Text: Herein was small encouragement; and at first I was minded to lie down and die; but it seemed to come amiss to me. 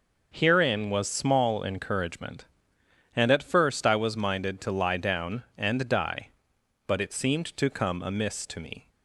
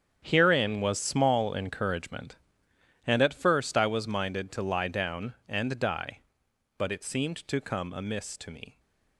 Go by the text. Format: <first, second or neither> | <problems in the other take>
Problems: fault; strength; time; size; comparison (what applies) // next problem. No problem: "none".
first | gets quieter; strong; throughout; 13.5 dB